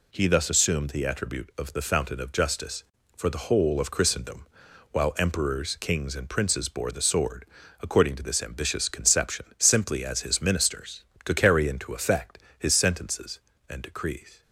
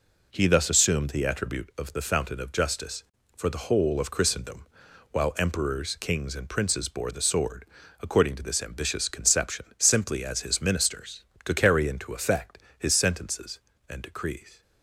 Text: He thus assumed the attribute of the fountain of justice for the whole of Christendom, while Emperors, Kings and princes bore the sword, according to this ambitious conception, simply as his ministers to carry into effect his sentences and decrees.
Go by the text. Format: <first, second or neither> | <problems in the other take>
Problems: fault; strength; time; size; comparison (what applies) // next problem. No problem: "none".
first | starts louder than the rest; noticeable; until 1.7 s; 4 dB // pauses between "effect" and "his"; slight; at 12.5 s; 0.20 s long; slight in the first